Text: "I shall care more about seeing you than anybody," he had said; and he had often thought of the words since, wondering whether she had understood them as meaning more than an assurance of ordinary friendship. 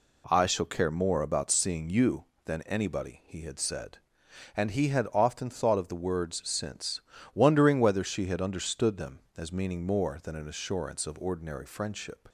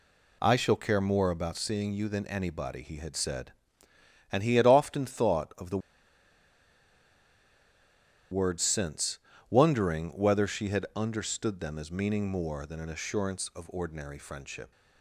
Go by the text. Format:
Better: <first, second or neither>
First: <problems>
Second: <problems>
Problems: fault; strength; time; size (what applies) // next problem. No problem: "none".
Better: first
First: none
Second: pauses between "the" and "words"; strong; at 5.7 s; 2.5 s long